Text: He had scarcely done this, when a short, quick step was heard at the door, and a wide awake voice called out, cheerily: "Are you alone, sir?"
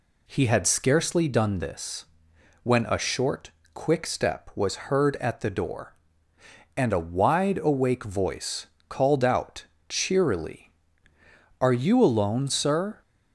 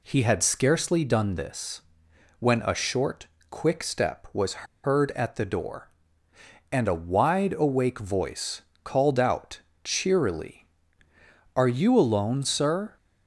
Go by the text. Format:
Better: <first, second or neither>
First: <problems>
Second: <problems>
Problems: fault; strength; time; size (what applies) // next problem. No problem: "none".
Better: first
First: pauses between "voice" and "called"; slight; at 8.6 s; 0.24 s long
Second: pauses between "was" and "heard"; slight; at 4.6 s; 0.18 s long // pauses between "voice" and "called"; slight; at 8.6 s; 0.24 s long